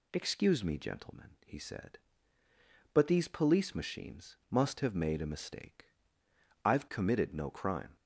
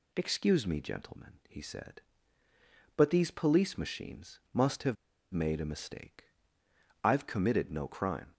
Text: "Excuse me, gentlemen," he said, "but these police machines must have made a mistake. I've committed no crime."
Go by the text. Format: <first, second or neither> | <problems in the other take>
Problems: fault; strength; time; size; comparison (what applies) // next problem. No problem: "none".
first | pauses between "have" and "made"; at 4.9 s; 0.39 s long